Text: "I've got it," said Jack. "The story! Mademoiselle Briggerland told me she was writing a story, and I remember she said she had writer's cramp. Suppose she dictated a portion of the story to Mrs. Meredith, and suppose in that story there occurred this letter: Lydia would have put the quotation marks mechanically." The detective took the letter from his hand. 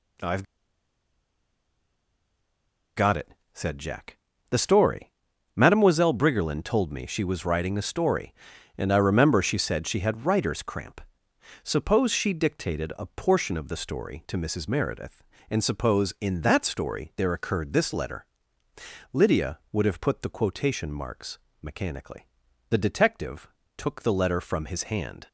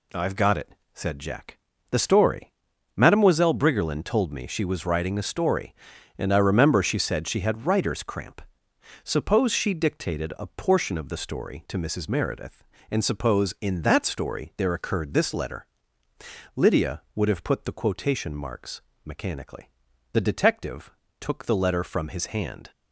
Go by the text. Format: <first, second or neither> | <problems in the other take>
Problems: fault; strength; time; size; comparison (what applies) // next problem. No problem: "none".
second | pauses between "I've" and "got"; strong; at 0.4 s; 2.5 s long // pauses between "marks" and "mechanically"; slight; at 21.3 s; 0.24 s long; slight in the second // pauses between "detective" and "took"; slight; at 23.4 s; 0.30 s long; slight in the second